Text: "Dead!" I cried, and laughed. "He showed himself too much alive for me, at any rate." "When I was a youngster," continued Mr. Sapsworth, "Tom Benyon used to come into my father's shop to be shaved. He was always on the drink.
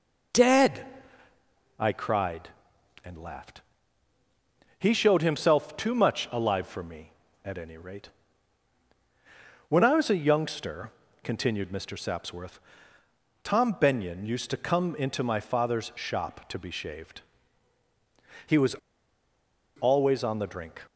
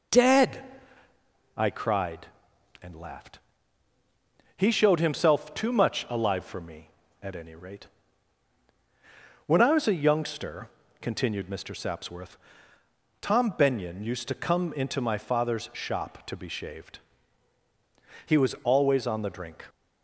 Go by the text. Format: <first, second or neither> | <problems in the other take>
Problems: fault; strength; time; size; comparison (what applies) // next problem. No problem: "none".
second | pauses between "was" and "always"; at 18.7 s; 1.0 s long